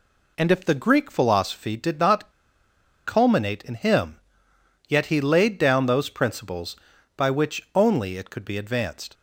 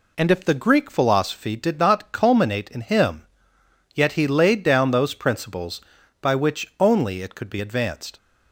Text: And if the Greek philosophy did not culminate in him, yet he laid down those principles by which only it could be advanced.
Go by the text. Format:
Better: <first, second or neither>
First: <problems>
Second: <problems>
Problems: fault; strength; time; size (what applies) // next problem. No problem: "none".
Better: second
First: pauses between "not" and "culminate"; noticeable; at 2.3 s; 0.74 s long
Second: none